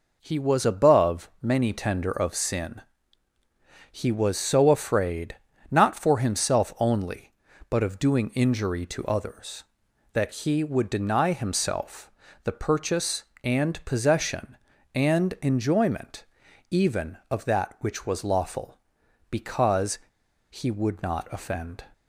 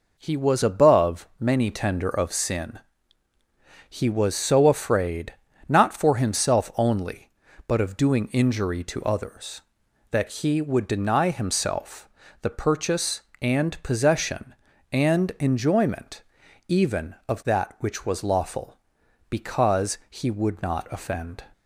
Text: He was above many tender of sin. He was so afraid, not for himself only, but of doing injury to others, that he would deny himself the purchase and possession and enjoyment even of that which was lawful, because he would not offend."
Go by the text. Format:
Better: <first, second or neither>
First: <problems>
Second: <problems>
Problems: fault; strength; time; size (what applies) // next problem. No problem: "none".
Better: second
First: pauses between "himself" and "the"; slight; at 12.1 s; 0.34 s long // pauses between "enjoyment" and "even"; noticeable; at 16.2 s; 0.48 s long // pauses between "because" and "he"; noticeable; at 19.9 s; 0.51 s long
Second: pauses between "himself" and "the"; slight; at 12.0 s; 0.34 s long // pauses between "enjoyment" and "even"; noticeable; at 16.2 s; 0.48 s long